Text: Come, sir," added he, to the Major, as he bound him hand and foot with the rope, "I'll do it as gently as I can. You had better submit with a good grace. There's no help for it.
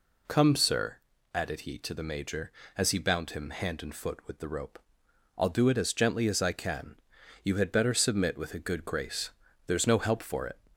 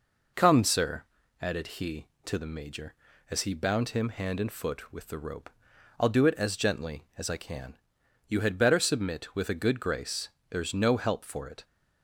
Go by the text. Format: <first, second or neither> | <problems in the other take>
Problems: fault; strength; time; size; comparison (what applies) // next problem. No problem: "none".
neither | none